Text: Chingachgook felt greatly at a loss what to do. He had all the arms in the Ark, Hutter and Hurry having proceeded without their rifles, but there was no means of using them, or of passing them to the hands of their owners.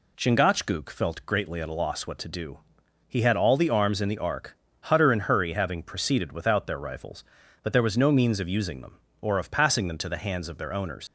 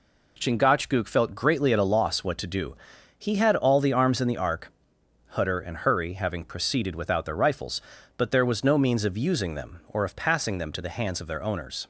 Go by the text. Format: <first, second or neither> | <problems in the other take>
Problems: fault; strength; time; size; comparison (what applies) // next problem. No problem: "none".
second | leaves "owners" unfinished; at 11.0 s; 75 ms